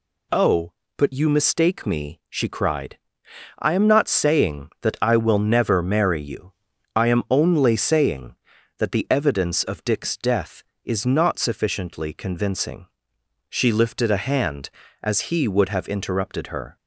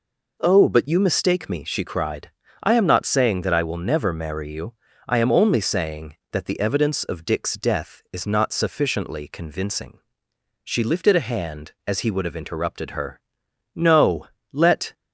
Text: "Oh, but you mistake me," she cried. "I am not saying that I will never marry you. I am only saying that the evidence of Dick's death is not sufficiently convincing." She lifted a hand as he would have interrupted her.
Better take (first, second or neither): first